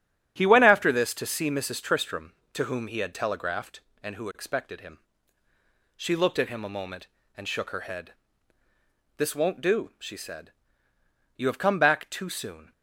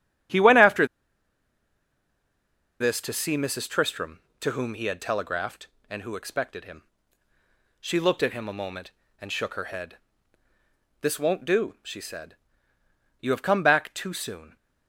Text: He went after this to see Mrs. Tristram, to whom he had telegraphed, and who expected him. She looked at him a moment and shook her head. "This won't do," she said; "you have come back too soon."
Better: first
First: starts louder than the rest; strong; until 1.3 s; 9 dB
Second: starts louder than the rest; strong; until 3.2 s; 9 dB // pauses between "after" and "this"; strong; at 0.8 s; 1.9 s long

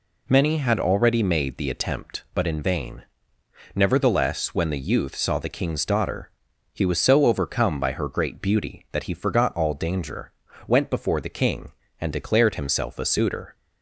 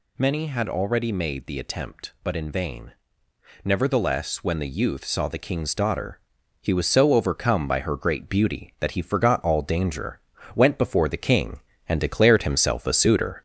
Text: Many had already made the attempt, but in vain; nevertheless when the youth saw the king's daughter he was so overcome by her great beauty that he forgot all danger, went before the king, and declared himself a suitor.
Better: first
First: pauses between "daughter" and "he"; at 6.3 s; 0.41 s long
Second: gets louder; throughout; 4 dB // pauses between "daughter" and "he"; at 6.1 s; 0.40 s long

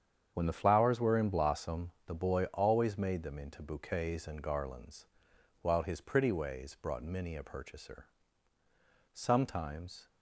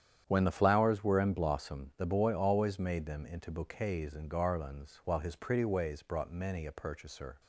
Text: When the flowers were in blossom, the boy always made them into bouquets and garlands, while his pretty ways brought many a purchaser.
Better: second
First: starts louder than the rest; strong; until 1.3 s; 8 dB // goes on to say "Sometimes"; noticeable; from 9.1 s on; 0.96 s long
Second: starts louder than the rest; strong; until 1.2 s; 9.5 dB

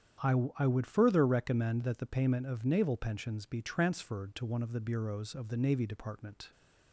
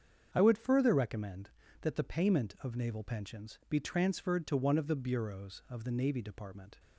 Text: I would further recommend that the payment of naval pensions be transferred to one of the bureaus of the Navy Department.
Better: second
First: starts louder than the rest; strong; until 1.4 s; 9 dB // says "I" twice; at 0.5 s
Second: starts louder than the rest; strong; until 1.3 s; 7 dB

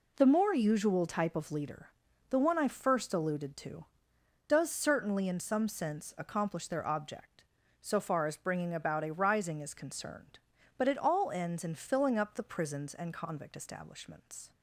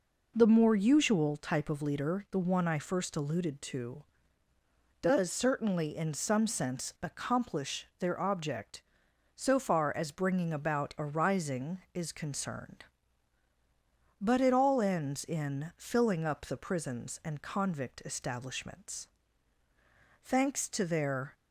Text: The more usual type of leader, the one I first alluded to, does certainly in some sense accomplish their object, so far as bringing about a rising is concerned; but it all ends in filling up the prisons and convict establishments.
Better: first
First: none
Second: goes on to say "Thanks to their"; noticeable; from 20.2 s on; 1.1 s long

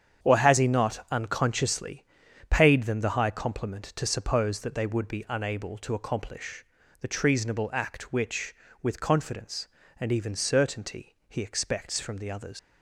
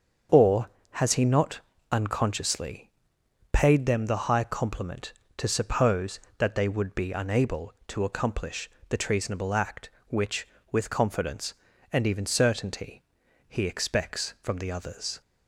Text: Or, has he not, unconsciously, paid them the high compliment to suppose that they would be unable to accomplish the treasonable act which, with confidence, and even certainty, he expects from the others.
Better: second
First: starts louder than the rest; strong; until 1.2 s; 8 dB // pauses between "accomplish" and "the"; slight; at 6.6 s; 0.36 s long // leaves "others" unfinished; at 12.5 s; 115 ms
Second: starts louder than the rest; until 1.5 s; 7 dB // pauses between "accomplish" and "the"; slight; at 8.7 s; 0.20 s long

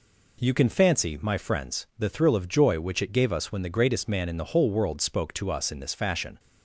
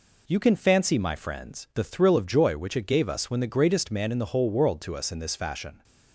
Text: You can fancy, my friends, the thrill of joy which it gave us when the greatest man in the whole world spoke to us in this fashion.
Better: first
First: none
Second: skips "spoke"; at 4.8 s

